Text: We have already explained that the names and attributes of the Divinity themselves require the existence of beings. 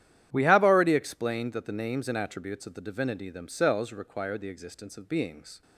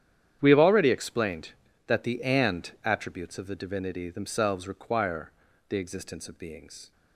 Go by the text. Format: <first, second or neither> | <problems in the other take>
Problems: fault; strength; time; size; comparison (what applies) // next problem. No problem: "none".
first | starts louder than the rest; strong; until 1.4 s; 10 dB; strong in the first // skips "names"; at 2.2 s // pauses between "require" and "the"; slight; at 5.3 s; 0.34 s long